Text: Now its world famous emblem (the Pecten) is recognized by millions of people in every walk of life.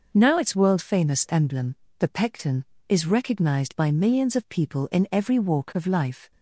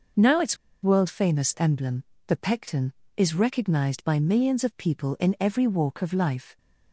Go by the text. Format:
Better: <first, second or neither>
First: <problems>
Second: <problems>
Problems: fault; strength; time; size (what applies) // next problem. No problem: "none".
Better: first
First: none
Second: pauses between "its" and "world"; slight; at 0.5 s; 0.26 s long